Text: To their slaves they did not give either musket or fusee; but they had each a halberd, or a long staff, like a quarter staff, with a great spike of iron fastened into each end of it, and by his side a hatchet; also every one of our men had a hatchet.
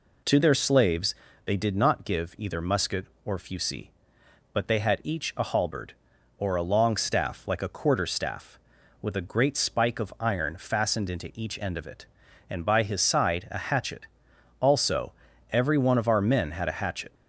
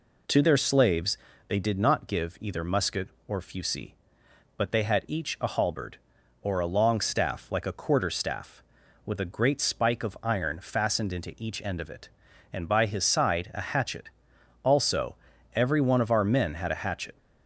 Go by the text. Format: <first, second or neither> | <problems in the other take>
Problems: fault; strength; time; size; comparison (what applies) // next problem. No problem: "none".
neither | pauses between "slaves" and "they"; slight; the same in both // pauses between "also" and "every"; the same in both